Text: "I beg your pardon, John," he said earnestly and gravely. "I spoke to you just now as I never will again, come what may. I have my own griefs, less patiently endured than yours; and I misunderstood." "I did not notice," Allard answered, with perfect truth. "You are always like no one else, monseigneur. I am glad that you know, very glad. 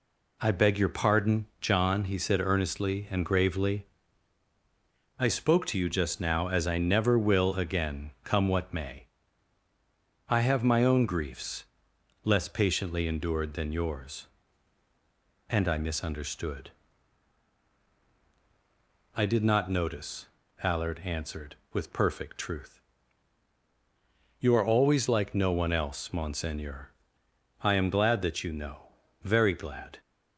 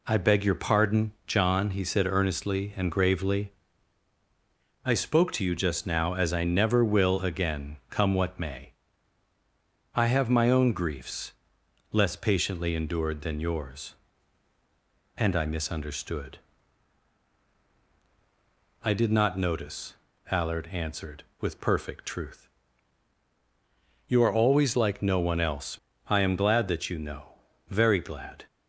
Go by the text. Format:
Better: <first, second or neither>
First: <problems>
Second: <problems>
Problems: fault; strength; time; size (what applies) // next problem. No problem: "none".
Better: first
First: none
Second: skips "monseigneur"; at 25.9 s